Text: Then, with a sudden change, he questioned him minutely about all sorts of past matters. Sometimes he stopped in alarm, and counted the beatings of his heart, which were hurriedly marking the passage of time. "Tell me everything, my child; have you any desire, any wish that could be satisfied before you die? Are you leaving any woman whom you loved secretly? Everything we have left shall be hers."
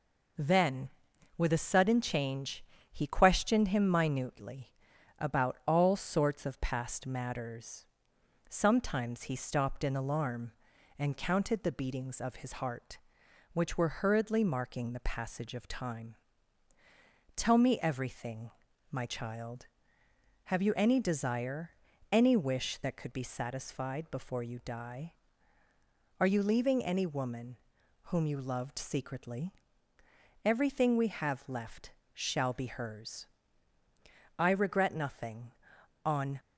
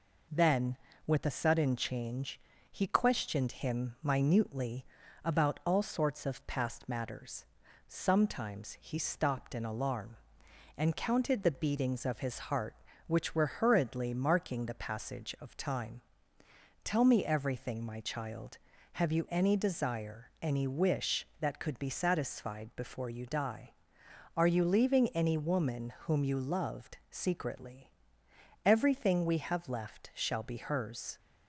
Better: second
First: pauses between "minutely" and "about"; at 4.7 s; 0.44 s long // pauses between "woman" and "whom"; noticeable; at 27.5 s; 0.46 s long // pauses between "left" and "shall"; slight; at 31.9 s; 0.22 s long // goes on to say "I regret nothing on"; strong; from 34.3 s on; 2.0 s long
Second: pauses between "minutely" and "about"; at 4.8 s; 0.40 s long

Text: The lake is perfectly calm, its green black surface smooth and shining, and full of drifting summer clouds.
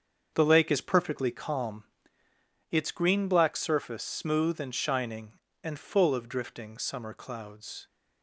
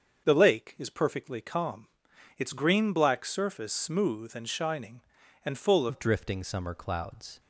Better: first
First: starts louder than the rest; until 1.3 s; 7 dB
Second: starts louder than the rest; until 1.2 s; 7 dB // changes voice at "of"; from 5.8 s on; 1.5 s long

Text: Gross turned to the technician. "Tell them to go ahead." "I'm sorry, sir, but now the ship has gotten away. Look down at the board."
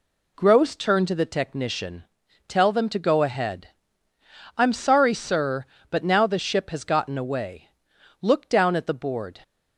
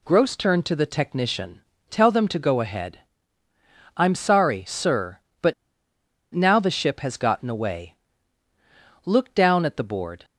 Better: first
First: none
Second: pauses between "but" and "now"; noticeable; at 5.5 s; 0.80 s long

